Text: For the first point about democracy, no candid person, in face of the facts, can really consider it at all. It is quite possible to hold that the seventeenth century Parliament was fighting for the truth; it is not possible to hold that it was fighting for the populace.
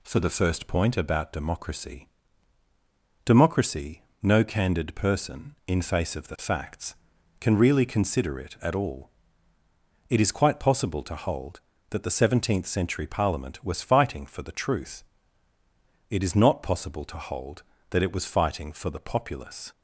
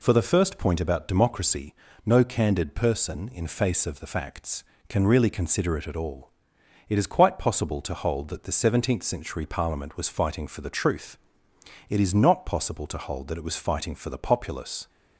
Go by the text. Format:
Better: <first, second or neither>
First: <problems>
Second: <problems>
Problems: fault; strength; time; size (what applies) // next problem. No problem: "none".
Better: second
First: says "democracy" twice; at 3.2 s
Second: none